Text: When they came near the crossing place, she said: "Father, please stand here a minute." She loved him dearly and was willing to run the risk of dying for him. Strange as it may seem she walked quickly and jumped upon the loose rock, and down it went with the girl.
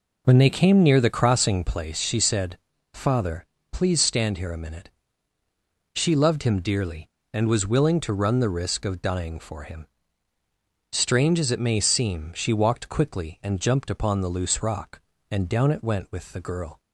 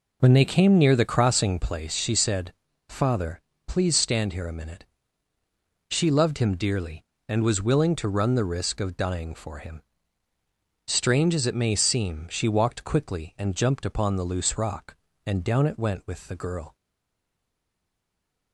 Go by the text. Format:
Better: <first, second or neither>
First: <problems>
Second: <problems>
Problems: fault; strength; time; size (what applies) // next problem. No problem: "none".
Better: first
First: none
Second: stays silent after the last word; noticeable; from 16.7 s on; 1.8 s long